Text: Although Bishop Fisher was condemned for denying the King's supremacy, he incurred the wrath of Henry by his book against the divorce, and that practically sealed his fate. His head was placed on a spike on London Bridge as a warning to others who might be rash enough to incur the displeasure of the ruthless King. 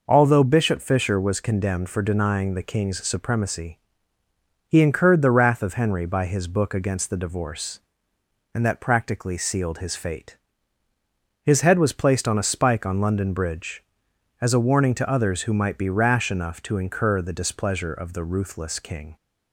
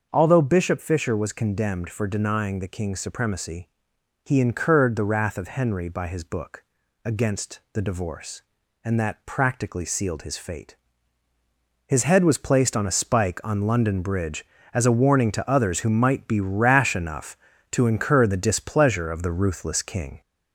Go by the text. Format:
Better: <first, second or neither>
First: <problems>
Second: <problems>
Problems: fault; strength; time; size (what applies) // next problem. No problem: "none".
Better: first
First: none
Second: gets louder; slight; throughout; 2.5 dB // starts louder than the rest; until 1.1 s; 6 dB // pauses between "book" and "against"; at 6.6 s; 0.40 s long